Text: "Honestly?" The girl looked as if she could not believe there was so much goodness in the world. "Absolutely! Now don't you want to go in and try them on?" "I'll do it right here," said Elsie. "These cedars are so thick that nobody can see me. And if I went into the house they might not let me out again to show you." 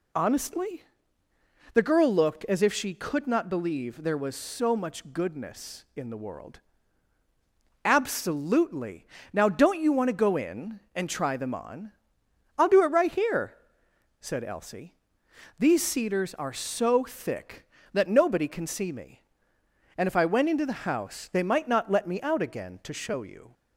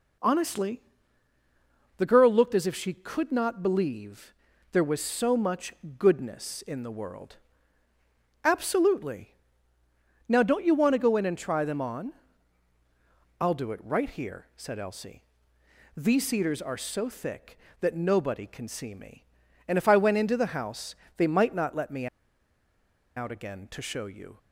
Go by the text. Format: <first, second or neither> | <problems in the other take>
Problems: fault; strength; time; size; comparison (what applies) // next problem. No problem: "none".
first | pauses between "believe" and "there"; at 4.3 s; 0.40 s long // pauses between "much" and "goodness"; slight; at 5.7 s; 0.24 s long // pauses between "house" and "they"; slight; at 20.9 s; 0.22 s long // pauses between "me" and "out"; at 22.0 s; 1.1 s long